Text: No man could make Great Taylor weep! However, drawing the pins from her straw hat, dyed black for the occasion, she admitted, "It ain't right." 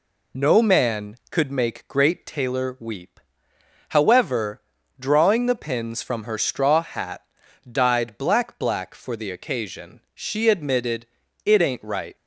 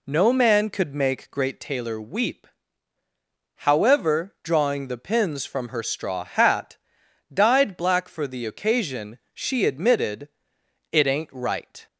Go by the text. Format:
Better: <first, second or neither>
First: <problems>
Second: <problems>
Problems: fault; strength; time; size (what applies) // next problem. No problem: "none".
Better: second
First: says "black" twice; at 8.5 s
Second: none